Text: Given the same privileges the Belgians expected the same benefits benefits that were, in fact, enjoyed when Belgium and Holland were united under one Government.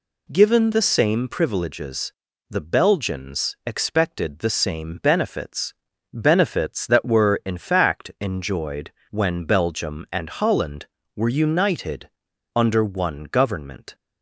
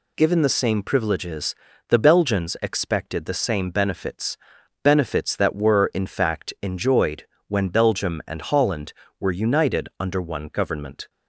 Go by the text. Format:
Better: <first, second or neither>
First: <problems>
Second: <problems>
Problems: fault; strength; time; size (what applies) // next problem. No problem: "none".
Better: second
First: pauses between "privileges" and "the"; at 2.1 s; 0.38 s long // pauses between "benefits" and "benefits"; at 5.7 s; 0.40 s long // pauses between "enjoyed" and "when"; slight; at 8.9 s; 0.20 s long // pauses between "united" and "under"; at 12.0 s; 0.45 s long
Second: pauses between "privileges" and "the"; slight; at 1.5 s; 0.34 s long // pauses between "benefits" and "benefits"; noticeable; at 4.3 s; 0.46 s long // pauses between "enjoyed" and "when"; slight; at 7.2 s; 0.20 s long